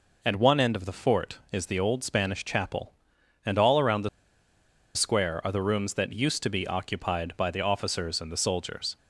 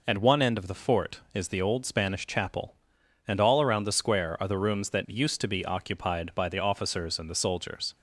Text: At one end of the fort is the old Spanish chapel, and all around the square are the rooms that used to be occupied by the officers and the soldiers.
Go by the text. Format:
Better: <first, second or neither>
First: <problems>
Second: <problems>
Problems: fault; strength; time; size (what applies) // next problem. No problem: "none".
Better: second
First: pauses between "the" and "square"; noticeable; at 4.0 s; 0.86 s long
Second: none